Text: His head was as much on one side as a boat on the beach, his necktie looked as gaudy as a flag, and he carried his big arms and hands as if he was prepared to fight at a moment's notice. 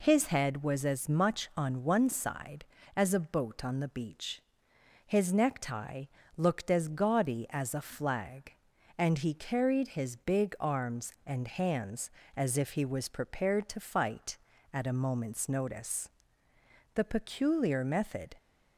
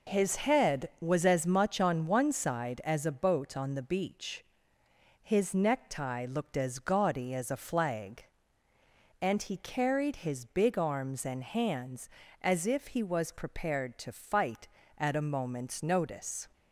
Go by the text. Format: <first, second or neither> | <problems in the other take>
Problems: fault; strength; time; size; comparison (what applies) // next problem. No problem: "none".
second | pauses between "necktie" and "looked"; slight; at 6.0 s; 0.32 s long // goes on to say "The peculiar method"; from 16.9 s on; 1.4 s long